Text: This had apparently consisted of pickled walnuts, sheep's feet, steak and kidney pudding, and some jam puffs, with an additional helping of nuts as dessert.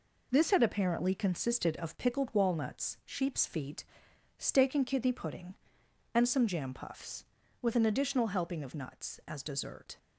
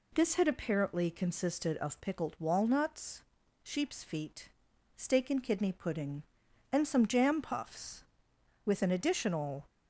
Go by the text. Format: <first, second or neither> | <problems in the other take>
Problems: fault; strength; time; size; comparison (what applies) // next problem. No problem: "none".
first | stops before "helping of nuts as dessert"; at 9.6 s